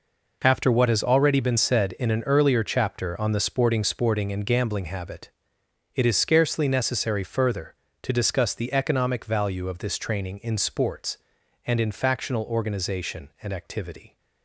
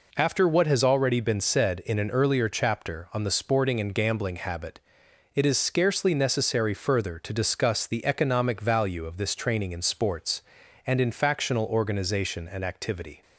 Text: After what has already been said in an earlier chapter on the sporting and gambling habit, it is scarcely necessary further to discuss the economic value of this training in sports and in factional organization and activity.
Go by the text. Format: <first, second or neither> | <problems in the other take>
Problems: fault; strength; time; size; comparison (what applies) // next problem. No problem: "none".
second | says "sporting" twice; at 3.8 s